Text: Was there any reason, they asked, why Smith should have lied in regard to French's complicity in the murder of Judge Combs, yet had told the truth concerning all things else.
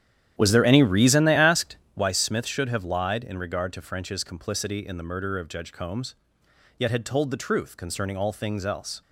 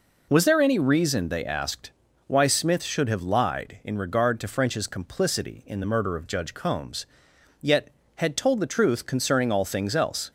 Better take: second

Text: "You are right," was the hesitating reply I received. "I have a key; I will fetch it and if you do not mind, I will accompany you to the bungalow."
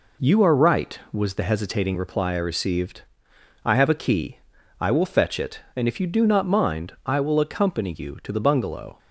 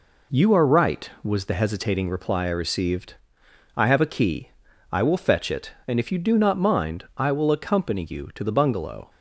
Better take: neither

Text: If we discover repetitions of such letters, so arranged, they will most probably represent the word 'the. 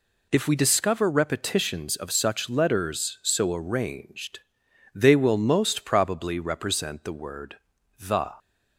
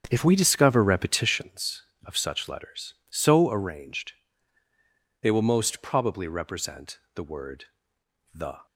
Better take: first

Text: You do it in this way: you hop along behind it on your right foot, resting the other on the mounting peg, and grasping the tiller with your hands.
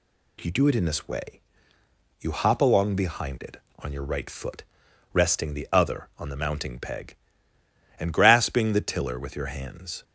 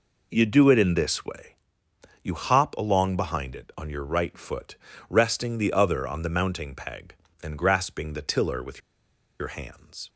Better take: first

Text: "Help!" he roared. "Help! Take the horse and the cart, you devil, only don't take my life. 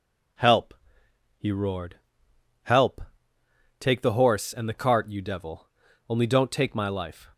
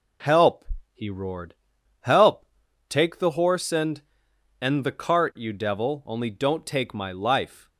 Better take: first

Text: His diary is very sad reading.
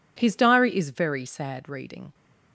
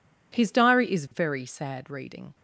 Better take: neither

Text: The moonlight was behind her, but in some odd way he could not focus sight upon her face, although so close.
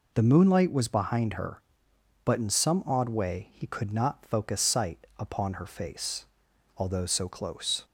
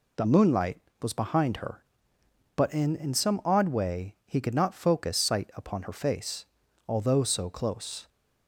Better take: first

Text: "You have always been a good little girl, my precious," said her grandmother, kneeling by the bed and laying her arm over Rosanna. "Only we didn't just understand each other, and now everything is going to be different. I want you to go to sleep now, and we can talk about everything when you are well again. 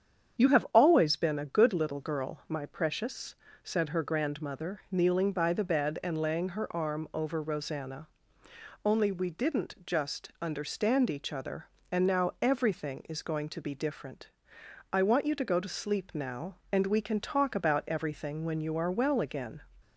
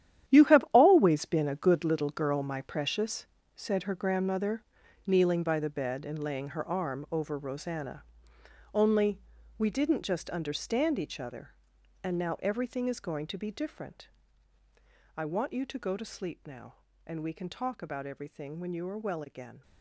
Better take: first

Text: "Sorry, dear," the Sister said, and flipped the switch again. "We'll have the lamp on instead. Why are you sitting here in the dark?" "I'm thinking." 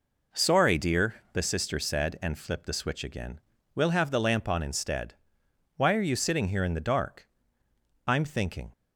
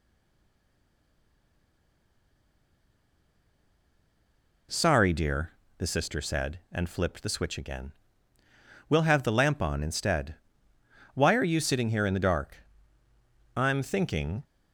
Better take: first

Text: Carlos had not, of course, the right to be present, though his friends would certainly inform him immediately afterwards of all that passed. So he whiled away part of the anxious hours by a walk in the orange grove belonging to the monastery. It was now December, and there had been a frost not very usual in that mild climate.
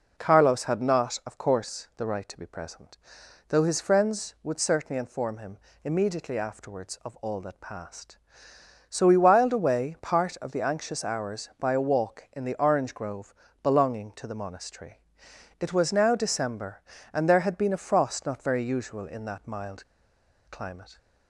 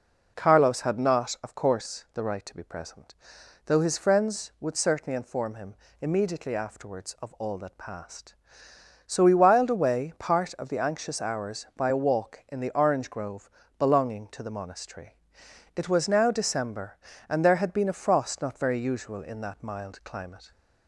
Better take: second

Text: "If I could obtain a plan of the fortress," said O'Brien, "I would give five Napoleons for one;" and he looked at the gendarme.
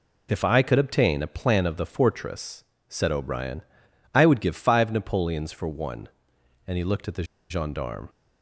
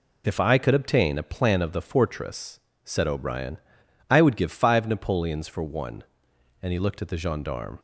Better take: second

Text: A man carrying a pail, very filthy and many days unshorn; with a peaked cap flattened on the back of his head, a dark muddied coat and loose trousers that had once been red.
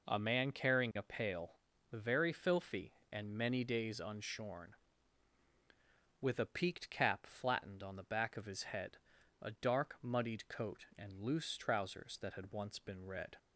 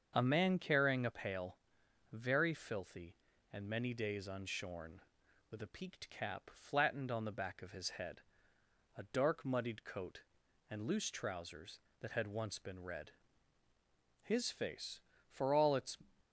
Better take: first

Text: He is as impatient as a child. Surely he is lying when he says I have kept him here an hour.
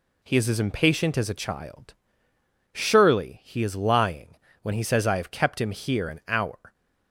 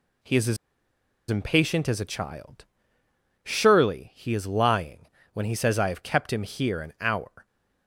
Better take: first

